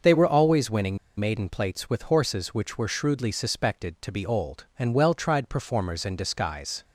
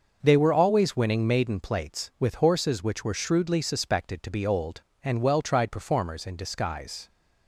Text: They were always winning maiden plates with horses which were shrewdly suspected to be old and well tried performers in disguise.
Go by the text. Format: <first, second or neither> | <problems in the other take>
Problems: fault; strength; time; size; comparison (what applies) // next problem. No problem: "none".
second | starts louder than the rest; until 1.2 s; 6 dB; noticeable in the second // pauses between "winning" and "maiden"; slight; at 0.9 s; 0.21 s long